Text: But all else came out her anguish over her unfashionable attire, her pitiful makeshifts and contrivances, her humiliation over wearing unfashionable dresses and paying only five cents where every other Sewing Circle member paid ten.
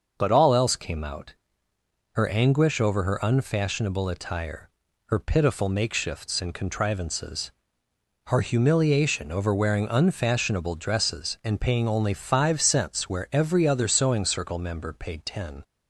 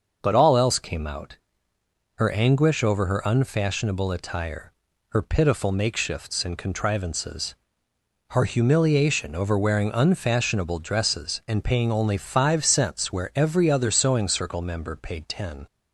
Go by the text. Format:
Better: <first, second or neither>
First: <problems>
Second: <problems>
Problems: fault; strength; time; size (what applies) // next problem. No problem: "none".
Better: neither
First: starts louder than the rest; until 1.1 s; 6 dB // pauses between "out" and "her"; noticeable; at 1.3 s; 0.80 s long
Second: starts louder than the rest; noticeable; until 1.2 s; 6 dB // pauses between "out" and "her"; noticeable; at 1.3 s; 0.80 s long